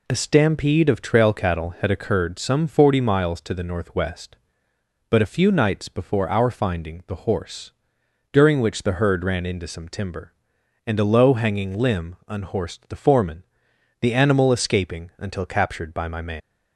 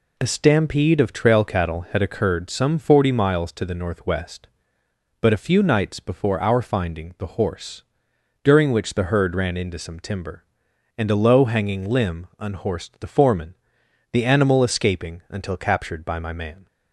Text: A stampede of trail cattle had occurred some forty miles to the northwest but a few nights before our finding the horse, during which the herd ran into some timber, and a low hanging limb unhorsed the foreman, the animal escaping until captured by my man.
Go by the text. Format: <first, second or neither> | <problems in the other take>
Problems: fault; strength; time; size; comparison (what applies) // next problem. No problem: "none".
second | leaves "man" unfinished; at 16.4 s; 155 ms